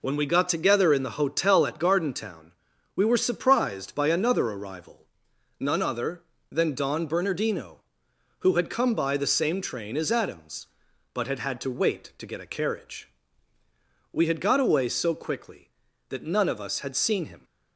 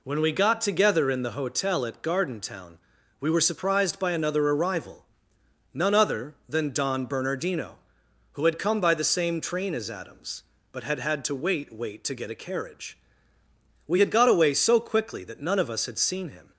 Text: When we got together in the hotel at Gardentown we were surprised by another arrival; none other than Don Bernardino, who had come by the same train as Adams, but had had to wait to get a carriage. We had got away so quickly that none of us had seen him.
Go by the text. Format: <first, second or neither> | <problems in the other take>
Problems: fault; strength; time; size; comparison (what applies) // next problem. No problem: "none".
first | pauses between "Gardentown" and "we"; at 2.7 s; 0.42 s long; also in the first // says "wait" twice; at 11.7 s